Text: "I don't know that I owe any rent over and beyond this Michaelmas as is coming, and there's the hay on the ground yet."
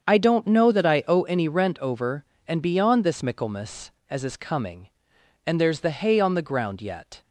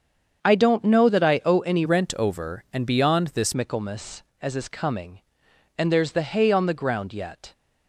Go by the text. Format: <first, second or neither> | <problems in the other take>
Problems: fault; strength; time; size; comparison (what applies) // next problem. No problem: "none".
first | starts louder than the rest; strong; until 1.4 s; 7 dB; strong in the first // changes voice from "rent" to "this"; from 1.8 to 3.5 s; 1.7 s long